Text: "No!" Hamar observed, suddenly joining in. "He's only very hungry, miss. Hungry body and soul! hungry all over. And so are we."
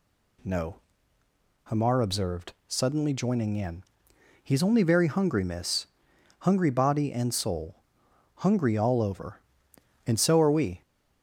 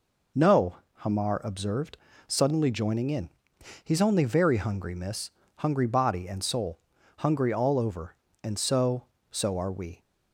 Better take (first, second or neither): first